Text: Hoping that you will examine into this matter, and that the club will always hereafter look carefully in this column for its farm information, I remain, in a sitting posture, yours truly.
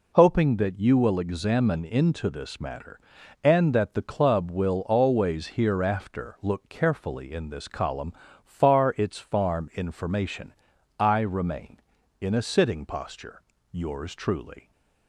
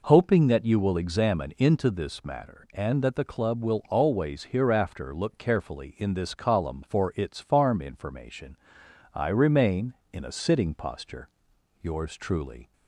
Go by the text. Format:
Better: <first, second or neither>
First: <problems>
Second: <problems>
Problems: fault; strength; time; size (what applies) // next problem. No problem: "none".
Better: second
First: says "far" for "for"; at 8.4 s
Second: none